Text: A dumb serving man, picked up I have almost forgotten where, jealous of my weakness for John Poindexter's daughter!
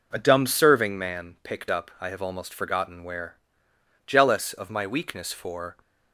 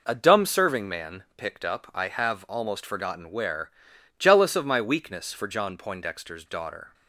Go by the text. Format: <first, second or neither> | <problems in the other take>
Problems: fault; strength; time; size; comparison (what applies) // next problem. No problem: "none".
second | stops before "John Poindexter's daughter"; at 5.8 s